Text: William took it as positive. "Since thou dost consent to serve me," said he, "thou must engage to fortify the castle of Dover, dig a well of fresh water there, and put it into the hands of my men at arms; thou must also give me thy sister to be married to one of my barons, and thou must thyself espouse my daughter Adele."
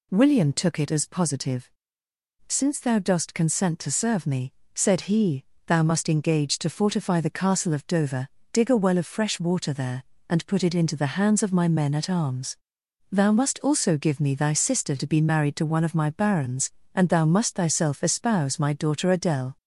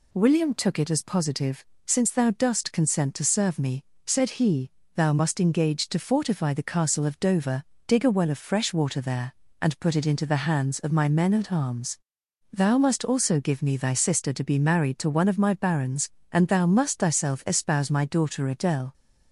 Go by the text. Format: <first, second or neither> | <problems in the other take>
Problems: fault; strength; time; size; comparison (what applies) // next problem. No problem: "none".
neither | none